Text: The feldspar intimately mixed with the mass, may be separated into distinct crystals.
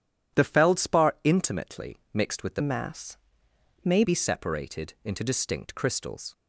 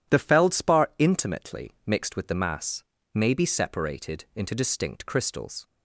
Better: second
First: changes voice from "mass" to "may"; from 2.6 to 4.0 s; 1.4 s long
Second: none

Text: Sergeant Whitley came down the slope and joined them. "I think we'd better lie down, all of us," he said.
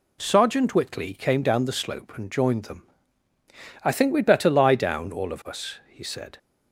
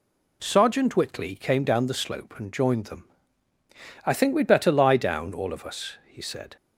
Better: neither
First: none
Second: none

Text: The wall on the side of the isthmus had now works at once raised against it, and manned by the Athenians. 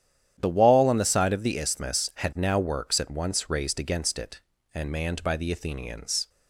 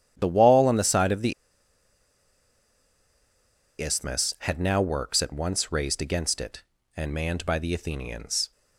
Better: first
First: starts louder than the rest; strong; until 1.3 s; 10 dB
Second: starts louder than the rest; strong; until 1.1 s; 10 dB // pauses between "the" and "isthmus"; strong; at 1.3 s; 2.4 s long

